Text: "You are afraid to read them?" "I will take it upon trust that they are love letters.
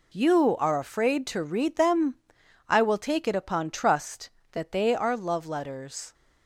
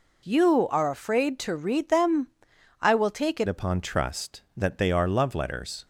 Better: first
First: none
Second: changes voice at "upon"; from 3.4 s on; 2.4 s long

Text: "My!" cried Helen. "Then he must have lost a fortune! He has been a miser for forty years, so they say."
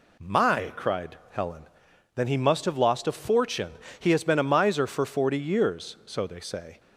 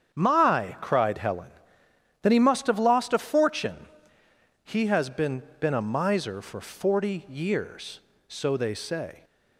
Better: first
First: none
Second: starts louder than the rest; strong; until 1.1 s; 8 dB // says "been" twice; at 5.6 s

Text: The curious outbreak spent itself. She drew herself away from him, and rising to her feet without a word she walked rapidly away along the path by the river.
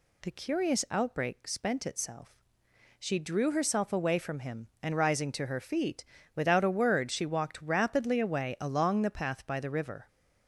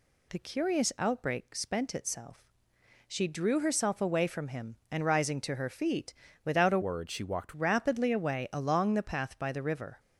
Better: first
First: pauses between "feet" and "without"; slight; at 6.0 s; 0.30 s long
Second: pauses between "feet" and "without"; slight; at 6.1 s; 0.30 s long // changes voice from "word" to "walked"; from 6.8 to 7.5 s; 0.7 s long

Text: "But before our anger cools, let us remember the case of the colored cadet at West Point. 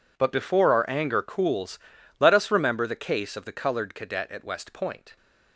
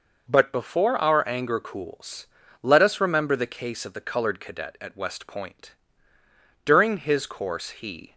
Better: first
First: none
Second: goes on to say "During his course he"; from 6.6 s on; 1.5 s long

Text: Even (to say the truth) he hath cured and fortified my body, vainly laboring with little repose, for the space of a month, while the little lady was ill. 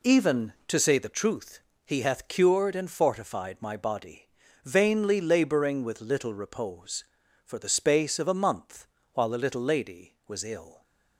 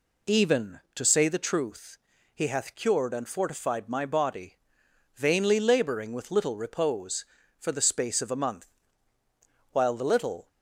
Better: first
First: none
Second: stops before "lady was ill"; at 10.4 s

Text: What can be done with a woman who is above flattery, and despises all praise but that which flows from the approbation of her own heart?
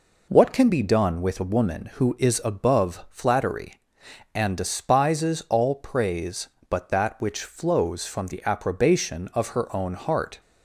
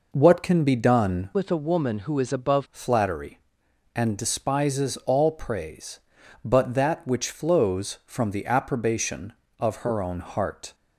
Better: first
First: none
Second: changes voice from "with" to "above"; from 1.3 to 2.6 s; 1.3 s long

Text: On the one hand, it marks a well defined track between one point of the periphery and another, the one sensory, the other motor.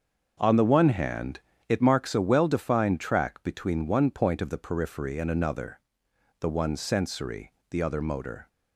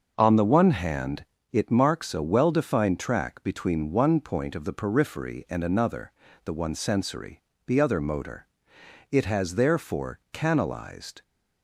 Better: first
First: starts louder than the rest; until 1.4 s; 6.5 dB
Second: starts louder than the rest; until 1.1 s; 6.5 dB // goes on to say "It has therefore canalized"; strong; from 9.1 s on; 2.1 s long

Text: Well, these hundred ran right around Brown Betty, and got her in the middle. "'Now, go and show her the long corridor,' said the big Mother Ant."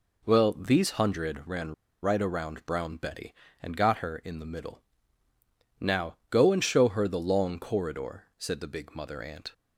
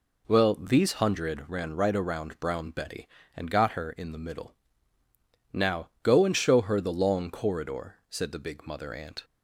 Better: second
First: pauses between "ran" and "right"; slight; at 1.7 s; 0.28 s long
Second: none

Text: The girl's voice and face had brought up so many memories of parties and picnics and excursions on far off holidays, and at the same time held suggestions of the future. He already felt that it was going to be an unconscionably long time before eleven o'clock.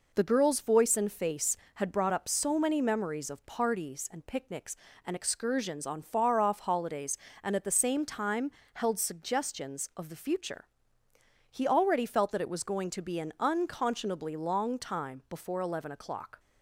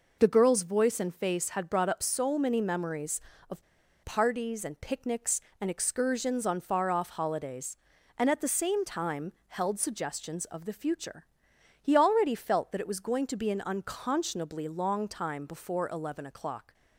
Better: first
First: pauses between "time" and "held"; slight; at 8.4 s; 0.24 s long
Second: pauses between "of" and "parties"; at 3.6 s; 0.41 s long // pauses between "time" and "held"; slight; at 9.3 s; 0.16 s long

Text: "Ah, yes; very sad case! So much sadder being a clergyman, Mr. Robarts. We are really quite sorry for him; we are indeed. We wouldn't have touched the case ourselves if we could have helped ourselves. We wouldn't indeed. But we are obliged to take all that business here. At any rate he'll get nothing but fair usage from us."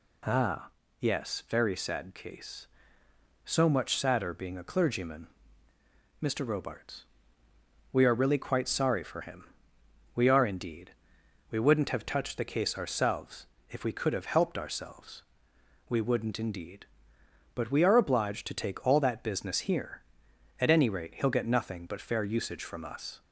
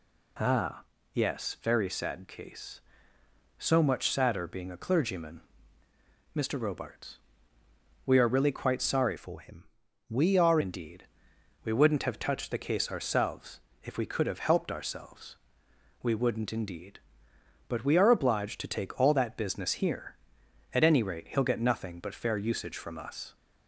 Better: first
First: pauses between "ourselves" and "if"; slight; at 13.4 s; 0.24 s long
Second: changes voice from "for" to "are"; from 9.1 to 10.5 s; 1.4 s long // pauses between "ourselves" and "if"; slight; at 13.6 s; 0.24 s long

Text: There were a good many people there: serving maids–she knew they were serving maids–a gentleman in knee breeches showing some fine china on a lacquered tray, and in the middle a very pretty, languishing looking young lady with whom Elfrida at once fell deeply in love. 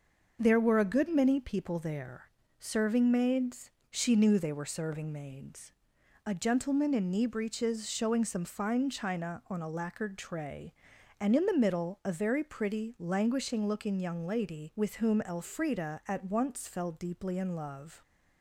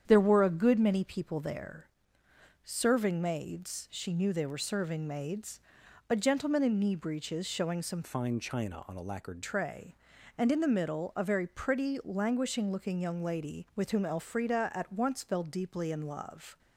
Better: first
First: starts louder than the rest; noticeable; until 1.4 s; 6 dB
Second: starts louder than the rest; strong; until 1.0 s; 8.5 dB // changes voice from "fine" to "lacquered"; from 8.0 to 9.4 s; 1.4 s long

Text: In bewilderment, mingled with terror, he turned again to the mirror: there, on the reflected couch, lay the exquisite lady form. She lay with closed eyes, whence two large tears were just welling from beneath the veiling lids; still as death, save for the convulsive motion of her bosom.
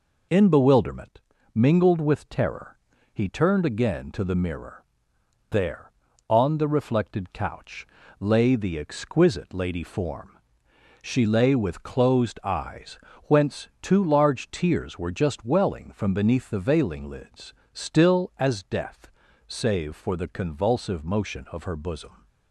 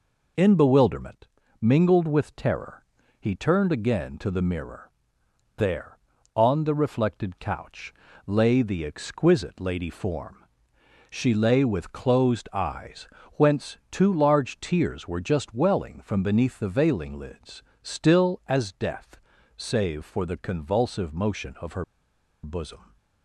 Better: first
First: none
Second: pauses between "her" and "bosom"; noticeable; at 21.8 s; 0.60 s long

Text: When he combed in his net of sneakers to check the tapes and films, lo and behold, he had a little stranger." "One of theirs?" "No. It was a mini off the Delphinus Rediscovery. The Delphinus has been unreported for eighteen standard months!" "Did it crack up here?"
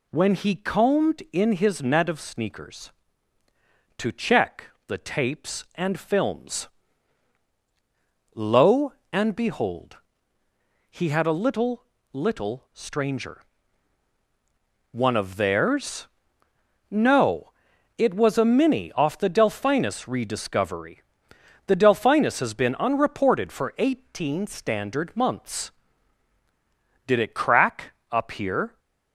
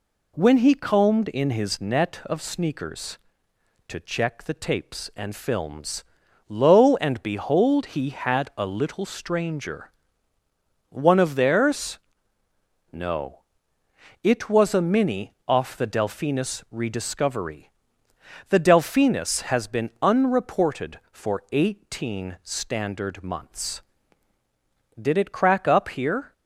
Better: second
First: pauses between "check" and "the"; slight; at 4.6 s; 0.22 s long // says "little" twice; at 12.1 s // pauses between "crack" and "up"; slight; at 27.9 s; 0.18 s long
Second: none

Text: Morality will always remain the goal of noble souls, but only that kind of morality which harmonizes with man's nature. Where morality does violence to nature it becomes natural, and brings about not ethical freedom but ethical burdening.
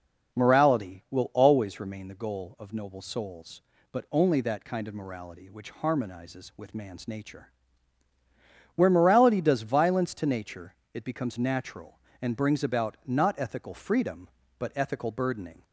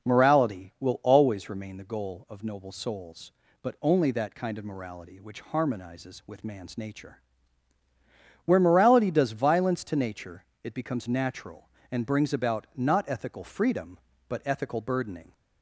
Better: neither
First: pauses between "nature" and "it"; slight; at 10.7 s; 0.20 s long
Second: pauses between "nature" and "it"; slight; at 10.4 s; 0.20 s long

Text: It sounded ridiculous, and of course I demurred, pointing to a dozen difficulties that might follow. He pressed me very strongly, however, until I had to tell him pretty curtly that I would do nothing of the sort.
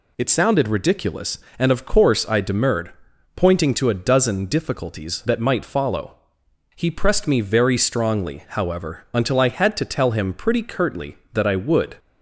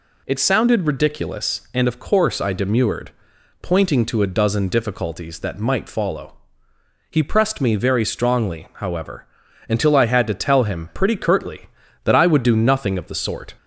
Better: second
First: stops before "do nothing of the sort"; at 11.9 s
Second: none

